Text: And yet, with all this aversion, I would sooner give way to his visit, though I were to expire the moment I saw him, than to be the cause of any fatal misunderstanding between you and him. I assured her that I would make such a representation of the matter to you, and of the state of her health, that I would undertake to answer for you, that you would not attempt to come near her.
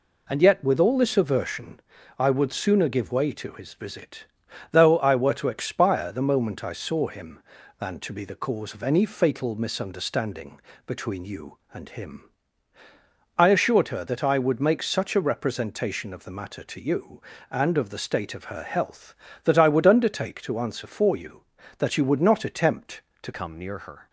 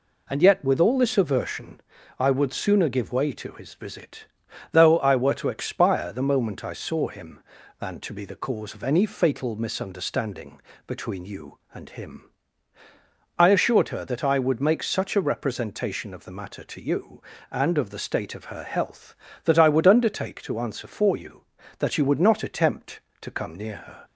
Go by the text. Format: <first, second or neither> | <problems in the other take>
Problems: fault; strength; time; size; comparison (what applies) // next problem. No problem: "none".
second | pauses between "misunderstanding" and "between"; slight; at 10.5 s; 0.26 s long; slight in the second // changes voice at "come"; from 23.3 s on; 0.7 s long